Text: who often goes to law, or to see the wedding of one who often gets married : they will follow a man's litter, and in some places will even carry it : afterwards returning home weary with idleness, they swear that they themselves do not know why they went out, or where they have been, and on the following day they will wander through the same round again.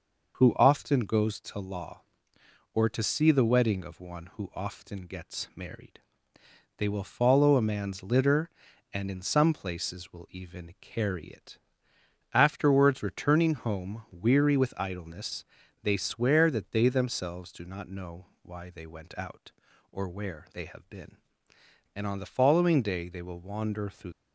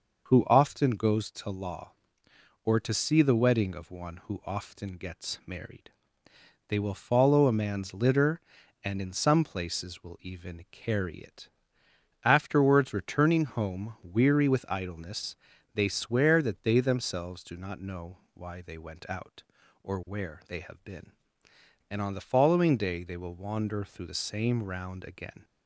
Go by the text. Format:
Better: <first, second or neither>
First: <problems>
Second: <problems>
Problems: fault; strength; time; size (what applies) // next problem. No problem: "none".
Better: second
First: pauses between "know" and "why"; slight; at 18.2 s; 0.18 s long // stops before "the same round again"; at 24.1 s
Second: pauses between "know" and "why"; slight; at 18.1 s; 0.18 s long